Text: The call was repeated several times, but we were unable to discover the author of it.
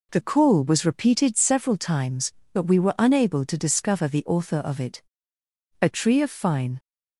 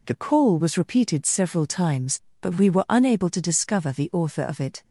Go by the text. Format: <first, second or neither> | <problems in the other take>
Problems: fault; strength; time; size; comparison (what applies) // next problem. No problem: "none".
second | goes on to say "A tree of fine"; noticeable; from 5.8 s on; 0.98 s long